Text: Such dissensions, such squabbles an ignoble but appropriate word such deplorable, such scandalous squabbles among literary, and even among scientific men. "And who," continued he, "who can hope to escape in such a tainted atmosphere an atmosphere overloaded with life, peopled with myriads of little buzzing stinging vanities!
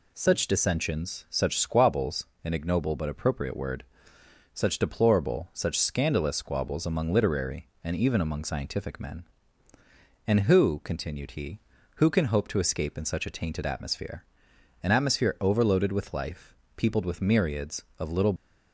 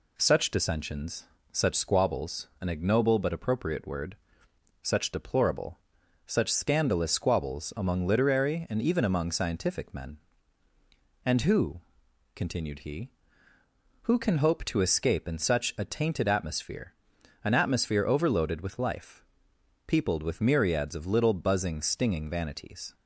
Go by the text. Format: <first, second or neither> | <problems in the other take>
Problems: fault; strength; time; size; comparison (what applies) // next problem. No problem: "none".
second | pauses between "squabbles" and "an"; slight; at 2.2 s; 0.18 s long // pauses between "word" and "such"; noticeable; at 3.8 s; 0.72 s long; noticeable in the second // pauses between "atmosphere" and "an"; noticeable; at 14.2 s; 0.60 s long; noticeable in the second // stops before "buzzing stinging vanities"; at 18.3 s